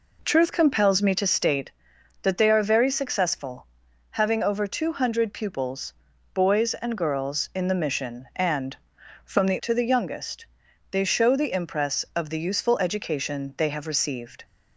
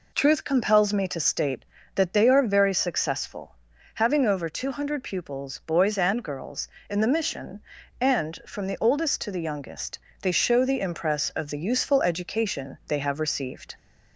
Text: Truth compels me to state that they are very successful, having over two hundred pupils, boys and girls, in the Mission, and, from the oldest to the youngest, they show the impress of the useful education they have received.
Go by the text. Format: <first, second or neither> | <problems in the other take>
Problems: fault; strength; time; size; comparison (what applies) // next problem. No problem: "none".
second | skips "oldest"; at 9.6 s